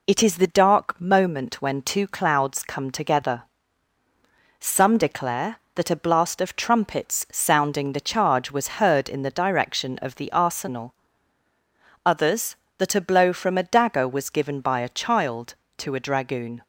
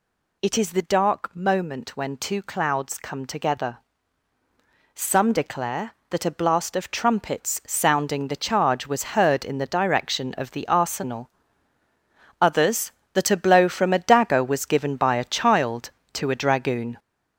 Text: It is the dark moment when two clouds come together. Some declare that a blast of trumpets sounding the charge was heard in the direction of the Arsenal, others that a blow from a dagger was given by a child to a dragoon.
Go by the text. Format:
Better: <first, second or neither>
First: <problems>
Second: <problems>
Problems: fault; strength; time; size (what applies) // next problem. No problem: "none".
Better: first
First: none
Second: gets louder; noticeable; throughout; 5.5 dB